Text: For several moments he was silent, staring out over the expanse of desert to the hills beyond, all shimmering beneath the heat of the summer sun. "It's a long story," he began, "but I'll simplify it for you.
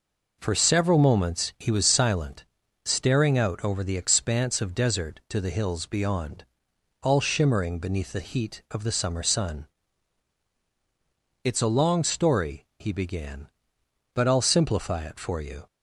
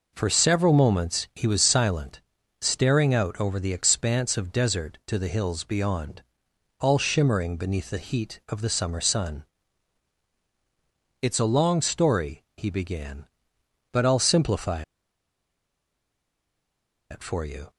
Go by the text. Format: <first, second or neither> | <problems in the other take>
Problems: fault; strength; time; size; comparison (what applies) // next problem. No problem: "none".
first | pauses between "simplify" and "it"; strong; at 14.8 s; 2.2 s long